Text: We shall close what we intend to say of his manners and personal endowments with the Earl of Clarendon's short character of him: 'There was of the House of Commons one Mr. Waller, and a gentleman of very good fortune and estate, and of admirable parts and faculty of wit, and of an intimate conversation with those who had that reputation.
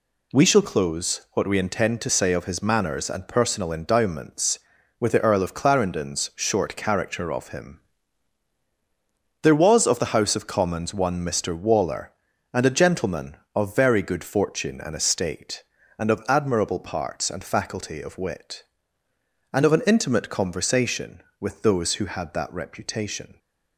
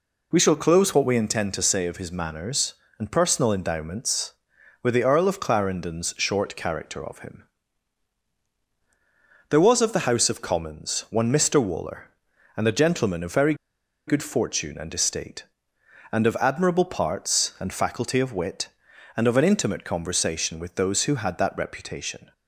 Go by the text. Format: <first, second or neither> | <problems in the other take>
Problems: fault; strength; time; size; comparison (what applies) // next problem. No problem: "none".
first | pauses between "very" and "good"; noticeable; at 13.5 s; 0.53 s long